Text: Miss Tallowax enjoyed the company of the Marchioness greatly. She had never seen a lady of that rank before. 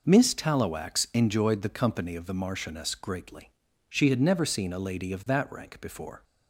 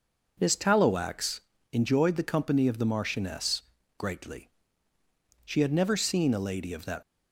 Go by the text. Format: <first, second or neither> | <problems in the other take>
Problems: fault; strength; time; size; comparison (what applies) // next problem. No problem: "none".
first | pauses between "Tallowax" and "enjoyed"; slight; at 1.4 s; 0.32 s long // pauses between "Marchioness" and "greatly"; slight; at 3.6 s; 0.36 s long // stops before "rank before"; at 7.0 s